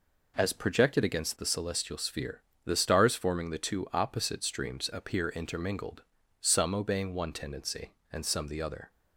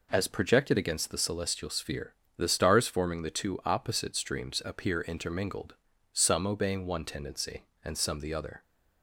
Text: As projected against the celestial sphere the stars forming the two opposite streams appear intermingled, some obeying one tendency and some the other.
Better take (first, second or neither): neither